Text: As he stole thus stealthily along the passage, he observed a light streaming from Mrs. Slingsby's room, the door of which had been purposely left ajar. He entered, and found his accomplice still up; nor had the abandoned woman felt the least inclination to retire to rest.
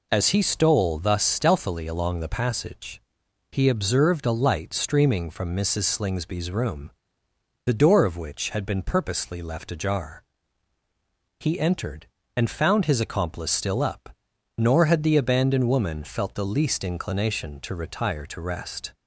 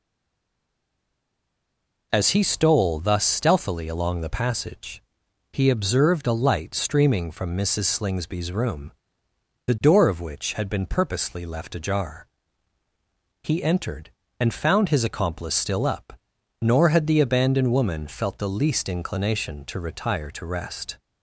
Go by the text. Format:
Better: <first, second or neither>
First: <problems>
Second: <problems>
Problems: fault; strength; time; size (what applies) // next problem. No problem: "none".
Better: first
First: none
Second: stays silent before the first word; until 2.1 s; 2.1 s long